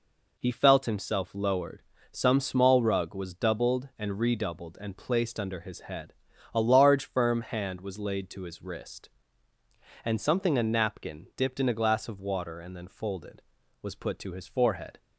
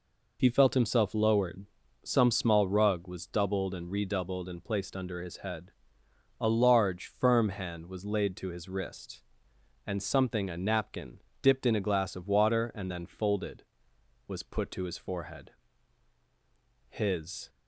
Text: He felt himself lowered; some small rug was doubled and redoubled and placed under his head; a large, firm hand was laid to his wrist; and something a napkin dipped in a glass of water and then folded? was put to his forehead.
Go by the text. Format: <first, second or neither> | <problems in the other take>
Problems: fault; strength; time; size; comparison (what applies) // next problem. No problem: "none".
first | pauses between "napkin" and "dipped"; slight; at 11.2 s; 0.22 s long // goes on to say "His"; noticeable; from 16.8 s on; 0.62 s long